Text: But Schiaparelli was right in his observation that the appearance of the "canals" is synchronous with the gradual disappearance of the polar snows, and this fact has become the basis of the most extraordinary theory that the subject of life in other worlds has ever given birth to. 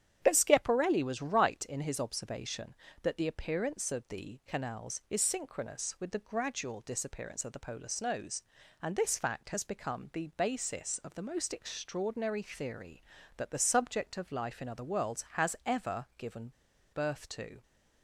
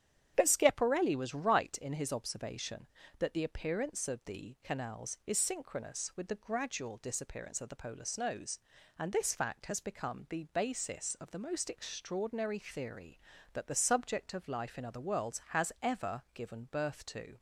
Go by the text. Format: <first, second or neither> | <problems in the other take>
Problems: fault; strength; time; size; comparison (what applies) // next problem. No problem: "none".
second | starts louder than the rest; strong; until 1.2 s; 9.5 dB; strong in the second // pauses between "given" and "birth"; at 16.5 s; 0.41 s long